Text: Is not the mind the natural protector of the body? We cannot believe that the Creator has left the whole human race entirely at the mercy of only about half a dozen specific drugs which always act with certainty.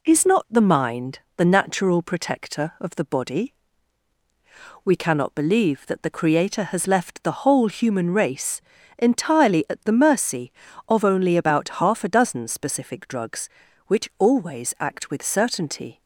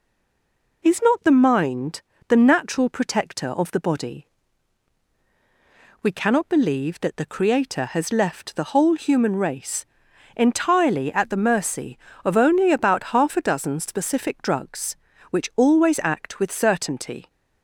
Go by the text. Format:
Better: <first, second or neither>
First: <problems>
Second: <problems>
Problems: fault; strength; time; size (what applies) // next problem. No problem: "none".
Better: first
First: pauses between "mind" and "the"; slight; at 1.1 s; 0.18 s long // pauses between "race" and "entirely"; slight; at 8.6 s; 0.34 s long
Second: stays silent before the first word; slight; until 0.8 s; 0.8 s long // pauses between "mind" and "the"; slight; at 2.0 s; 0.26 s long // pauses between "race" and "entirely"; noticeable; at 9.8 s; 0.50 s long